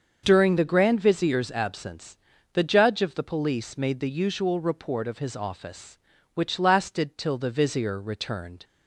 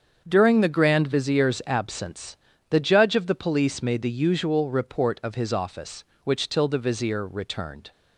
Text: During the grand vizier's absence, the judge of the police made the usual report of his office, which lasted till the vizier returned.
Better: first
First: starts louder than the rest; until 1.2 s; 6.5 dB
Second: starts louder than the rest; strong; until 1.2 s; 7 dB // skips "lasted"; at 6.4 s

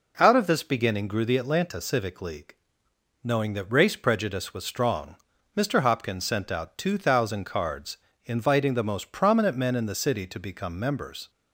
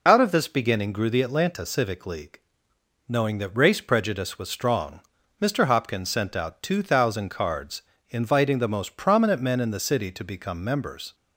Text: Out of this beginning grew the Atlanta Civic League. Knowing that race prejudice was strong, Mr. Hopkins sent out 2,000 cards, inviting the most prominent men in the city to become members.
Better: first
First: none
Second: loses the start of "Out"; at 0.0 s; 40 ms

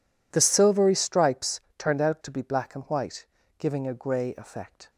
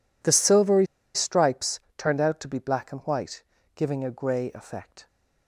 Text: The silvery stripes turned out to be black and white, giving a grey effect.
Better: first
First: pauses between "stripes" and "turned"; slight; at 1.5 s; 0.18 s long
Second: pauses between "silvery" and "stripes"; slight; at 0.8 s; 0.28 s long // pauses between "stripes" and "turned"; slight; at 1.7 s; 0.18 s long

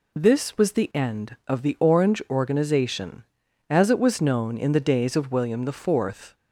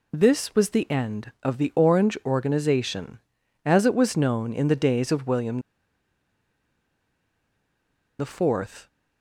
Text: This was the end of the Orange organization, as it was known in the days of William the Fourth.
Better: first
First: none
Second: pauses between "William" and "the"; strong; at 5.6 s; 2.5 s long

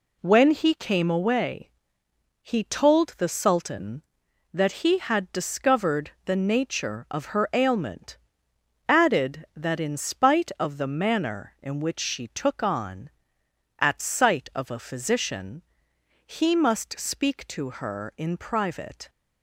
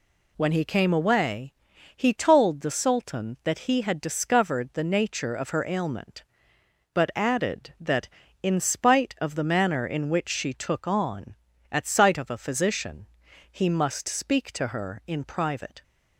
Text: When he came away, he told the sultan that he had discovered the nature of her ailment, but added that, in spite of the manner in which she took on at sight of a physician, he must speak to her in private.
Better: second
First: skips "but"; at 8.5 s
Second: none

